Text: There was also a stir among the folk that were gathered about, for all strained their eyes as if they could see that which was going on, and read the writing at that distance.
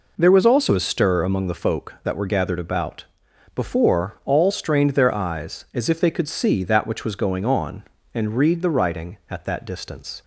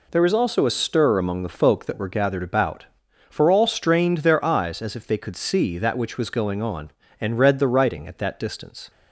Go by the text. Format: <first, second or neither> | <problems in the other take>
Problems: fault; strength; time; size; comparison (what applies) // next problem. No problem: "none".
second | says "before" for "for"; at 3.5 s